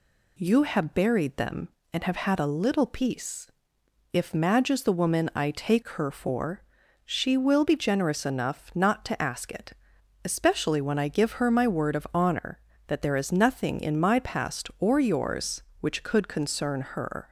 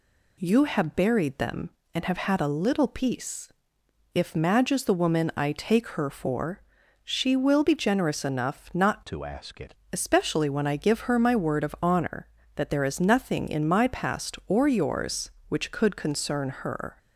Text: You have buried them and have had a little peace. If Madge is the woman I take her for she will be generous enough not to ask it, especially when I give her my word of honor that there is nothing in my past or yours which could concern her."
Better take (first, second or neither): first